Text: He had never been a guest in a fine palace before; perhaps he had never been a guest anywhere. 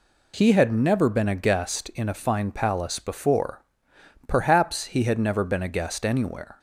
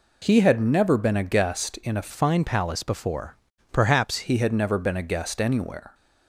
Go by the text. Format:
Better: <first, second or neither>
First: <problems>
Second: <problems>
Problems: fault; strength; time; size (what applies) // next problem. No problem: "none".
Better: first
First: none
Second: changes voice from "fine" to "perhaps"; from 2.0 to 4.2 s; 2.2 s long